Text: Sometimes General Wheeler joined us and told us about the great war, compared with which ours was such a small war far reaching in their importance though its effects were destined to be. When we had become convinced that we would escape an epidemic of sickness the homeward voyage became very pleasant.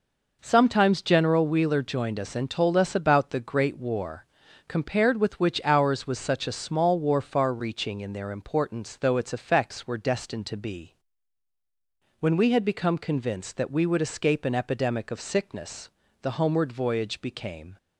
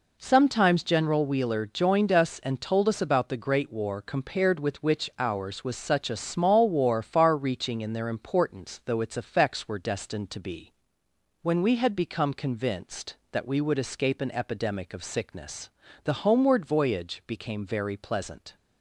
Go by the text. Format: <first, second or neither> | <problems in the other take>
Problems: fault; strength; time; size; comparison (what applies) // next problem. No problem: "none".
second | pauses between "sickness" and "the"; slight; at 15.8 s; 0.32 s long; slight in the second // stops before "very pleasant"; at 17.7 s